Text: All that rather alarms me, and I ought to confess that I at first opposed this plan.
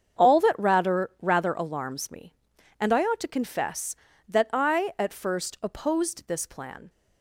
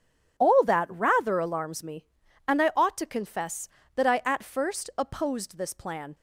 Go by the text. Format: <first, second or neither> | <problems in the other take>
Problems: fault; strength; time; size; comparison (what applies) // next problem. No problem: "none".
second | starts louder than the rest; strong; until 1.3 s; 7.5 dB // says "rather" twice; at 1.2 s